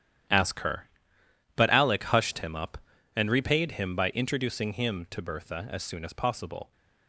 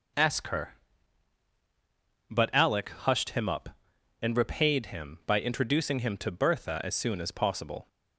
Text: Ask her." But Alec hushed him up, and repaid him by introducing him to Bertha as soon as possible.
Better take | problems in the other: second | gets quieter; strong; throughout; 12.5 dB

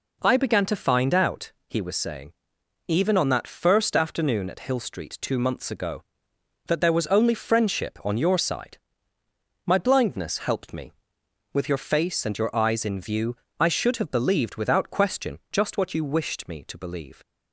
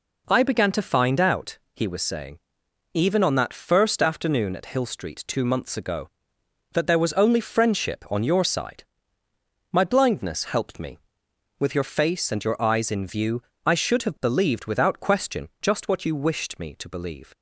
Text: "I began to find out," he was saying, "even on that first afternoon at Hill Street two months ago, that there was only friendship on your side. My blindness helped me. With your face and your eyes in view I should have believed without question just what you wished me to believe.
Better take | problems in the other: neither | pauses between "view" and "I"; slight; the same in both

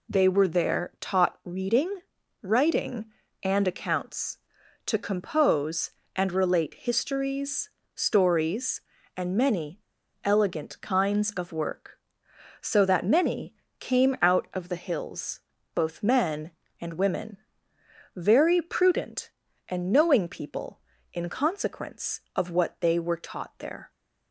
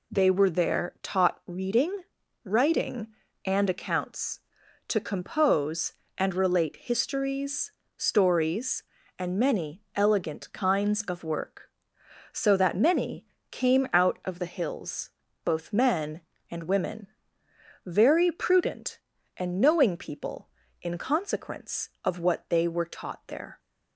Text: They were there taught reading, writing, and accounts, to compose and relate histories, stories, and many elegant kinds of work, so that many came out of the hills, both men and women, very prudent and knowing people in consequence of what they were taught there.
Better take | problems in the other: second | pauses between "many" and "elegant"; at 9.8 s; 0.42 s long // pauses between "many" and "came"; slight; at 13.5 s; 0.26 s long; slight in the second

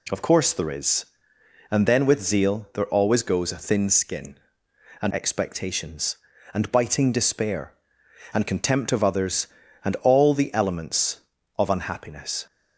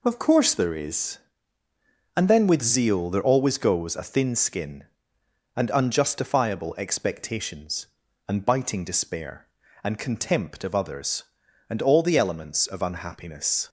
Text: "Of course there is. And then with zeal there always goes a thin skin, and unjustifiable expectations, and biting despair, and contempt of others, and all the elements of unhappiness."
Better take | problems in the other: second | skips "unjustifiable"; at 5.1 s

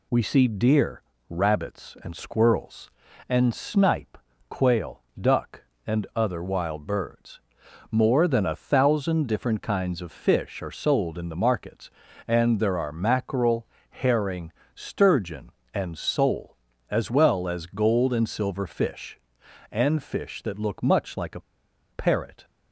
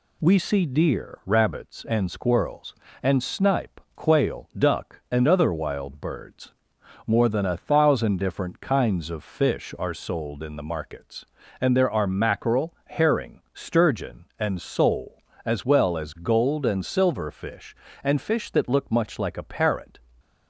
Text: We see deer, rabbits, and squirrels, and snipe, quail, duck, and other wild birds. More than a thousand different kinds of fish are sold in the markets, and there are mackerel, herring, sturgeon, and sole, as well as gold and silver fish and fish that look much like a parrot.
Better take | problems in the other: second | pauses between "a" and "parrot"; noticeable; at 21.3 s; 0.51 s long

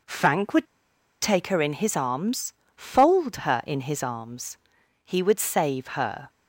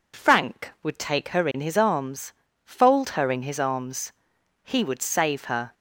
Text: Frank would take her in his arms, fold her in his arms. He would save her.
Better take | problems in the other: second | pauses between "would" and "take"; noticeable; at 0.6 s; 0.56 s long

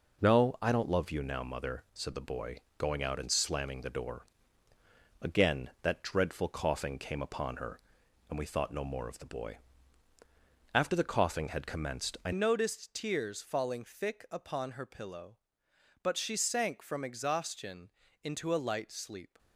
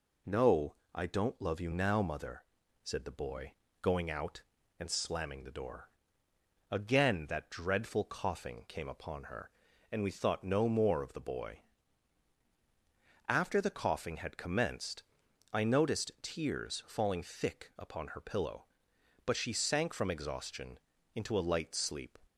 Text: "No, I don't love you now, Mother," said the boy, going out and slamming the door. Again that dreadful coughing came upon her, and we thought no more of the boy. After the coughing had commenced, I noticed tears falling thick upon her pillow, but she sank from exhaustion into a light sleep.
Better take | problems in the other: second | changes voice at "noticed"; from 12.3 s on; 7.0 s long // pauses between "exhaustion" and "into"; slight; at 17.8 s; 0.34 s long; also in the second

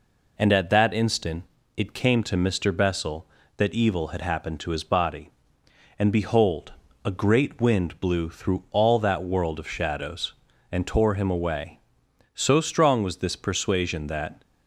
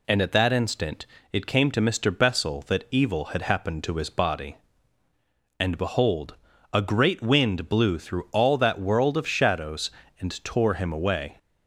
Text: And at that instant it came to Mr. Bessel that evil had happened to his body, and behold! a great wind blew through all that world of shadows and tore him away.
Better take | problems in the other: second | pauses between "instant" and "it"; slight; at 1.4 s; 0.32 s long; slight in the second // goes on to say "So strong was this persuasion that"; strong; from 12.3 s on; 2.0 s long

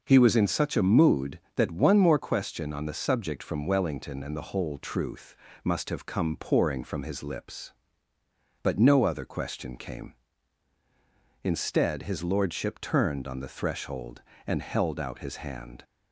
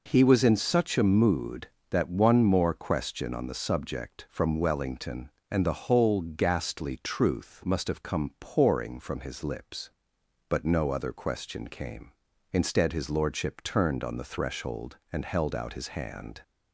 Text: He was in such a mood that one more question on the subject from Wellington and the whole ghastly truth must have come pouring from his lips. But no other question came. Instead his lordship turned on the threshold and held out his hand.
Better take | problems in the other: second | skips "ghastly"; at 4.7 s // pauses between "truth" and "must"; slight; at 5.3 s; 0.28 s long

